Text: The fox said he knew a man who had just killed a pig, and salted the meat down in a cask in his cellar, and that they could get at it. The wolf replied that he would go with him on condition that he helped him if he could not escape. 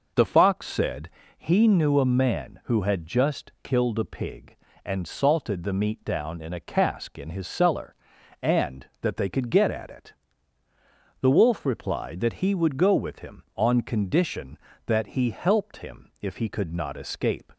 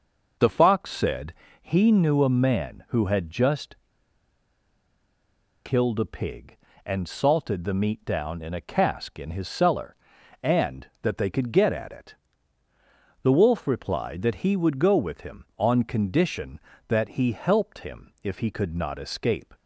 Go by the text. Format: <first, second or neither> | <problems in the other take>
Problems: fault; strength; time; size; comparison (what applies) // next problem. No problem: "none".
first | pauses between "said" and "he"; slight; at 1.3 s; 0.28 s long; slight in the first // pauses between "just" and "killed"; strong; at 3.7 s; 1.9 s long